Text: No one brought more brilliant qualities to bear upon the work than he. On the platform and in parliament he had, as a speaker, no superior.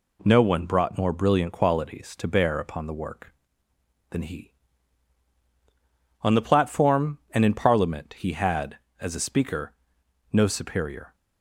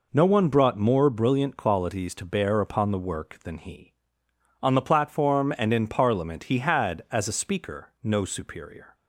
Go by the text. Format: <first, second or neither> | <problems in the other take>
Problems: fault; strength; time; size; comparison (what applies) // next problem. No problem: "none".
neither | none